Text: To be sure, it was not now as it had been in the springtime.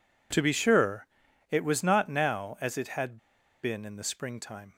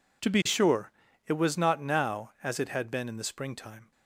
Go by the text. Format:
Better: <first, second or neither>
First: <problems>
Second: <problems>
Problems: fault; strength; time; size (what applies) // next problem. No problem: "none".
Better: second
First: pauses between "had" and "been"; at 3.1 s; 0.45 s long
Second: none